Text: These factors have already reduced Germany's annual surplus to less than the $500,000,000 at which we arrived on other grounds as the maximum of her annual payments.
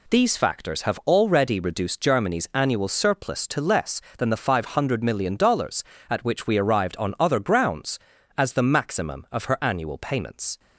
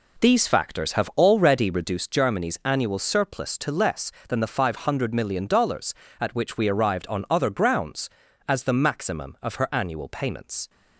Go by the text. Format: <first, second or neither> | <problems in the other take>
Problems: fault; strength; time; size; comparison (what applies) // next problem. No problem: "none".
first | starts louder than the rest; slight; until 2.0 s; 2.5 dB